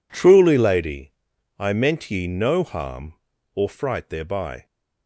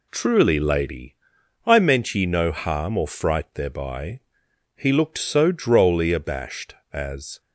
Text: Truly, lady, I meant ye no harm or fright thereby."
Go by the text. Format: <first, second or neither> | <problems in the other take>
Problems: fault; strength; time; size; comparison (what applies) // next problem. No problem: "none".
first | goes on to say "He looked so drolly abashed as"; strong; from 4.7 s on; 2.6 s long